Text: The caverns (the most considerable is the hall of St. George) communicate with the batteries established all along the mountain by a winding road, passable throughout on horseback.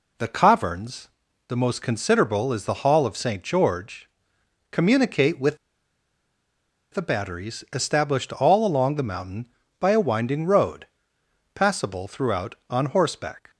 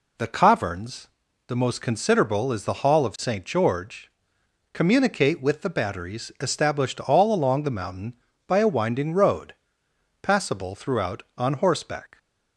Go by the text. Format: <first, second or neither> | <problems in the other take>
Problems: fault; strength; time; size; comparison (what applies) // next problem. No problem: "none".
second | pauses between "with" and "the"; strong; at 5.5 s; 1.3 s long